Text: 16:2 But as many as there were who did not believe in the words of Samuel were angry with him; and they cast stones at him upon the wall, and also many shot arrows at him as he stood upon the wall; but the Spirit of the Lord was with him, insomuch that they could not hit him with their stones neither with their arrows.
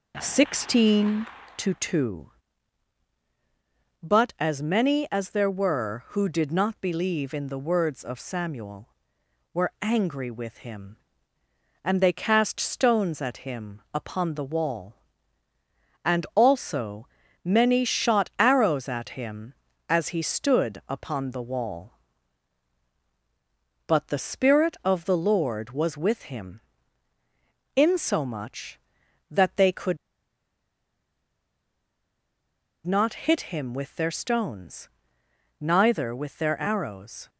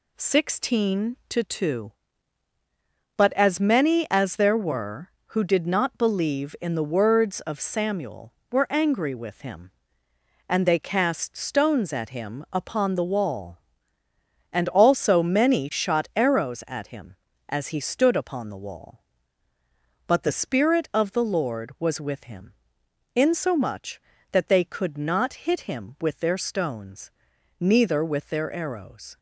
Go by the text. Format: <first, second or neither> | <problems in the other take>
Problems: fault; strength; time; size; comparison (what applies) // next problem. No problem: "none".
second | pauses between "also" and "many"; at 17.0 s; 0.38 s long // pauses between "could" and "not"; strong; at 29.9 s; 2.8 s long // pauses between "stones" and "neither"; noticeable; at 34.8 s; 0.72 s long; noticeable in the second